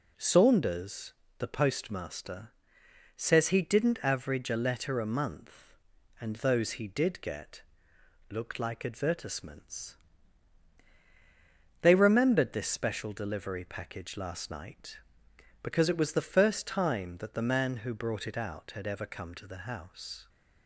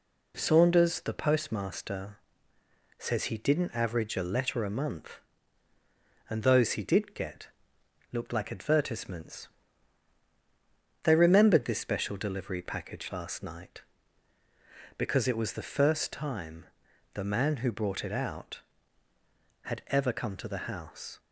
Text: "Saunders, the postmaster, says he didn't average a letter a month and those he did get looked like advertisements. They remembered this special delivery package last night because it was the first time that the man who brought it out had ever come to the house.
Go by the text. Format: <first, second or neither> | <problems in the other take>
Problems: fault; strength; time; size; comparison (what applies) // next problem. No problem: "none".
first | pauses between "get" and "looked"; noticeable; at 7.4 s; 0.64 s long; noticeable in the first // skips "that"; at 16.8 s